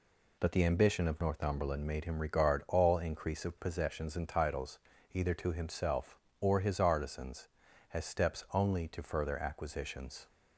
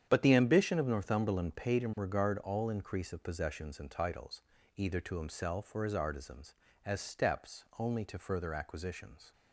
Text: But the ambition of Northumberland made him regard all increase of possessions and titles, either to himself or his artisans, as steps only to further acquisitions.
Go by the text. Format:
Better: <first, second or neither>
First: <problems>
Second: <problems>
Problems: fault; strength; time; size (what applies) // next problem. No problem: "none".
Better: first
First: none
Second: starts louder than the rest; strong; until 1.0 s; 9 dB // says "paid" for "made"; at 1.5 s